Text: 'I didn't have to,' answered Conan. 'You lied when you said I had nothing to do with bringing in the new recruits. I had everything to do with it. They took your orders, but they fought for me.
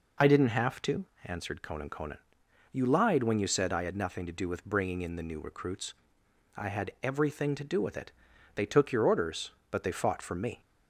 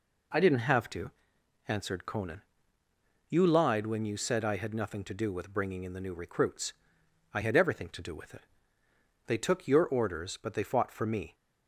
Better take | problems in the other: second | says "Conan" twice; at 1.8 s

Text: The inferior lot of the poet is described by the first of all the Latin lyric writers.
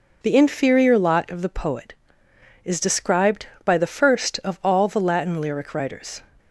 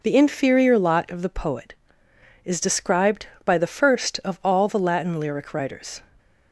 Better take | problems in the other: neither | none

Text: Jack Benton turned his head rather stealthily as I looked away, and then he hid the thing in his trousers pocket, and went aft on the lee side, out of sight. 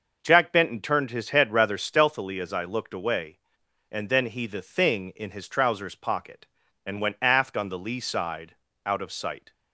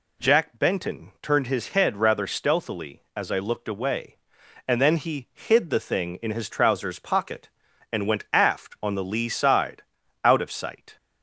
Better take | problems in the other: second | starts louder than the rest; noticeable; until 1.2 s; 6 dB // skips "hid"; at 4.4 s

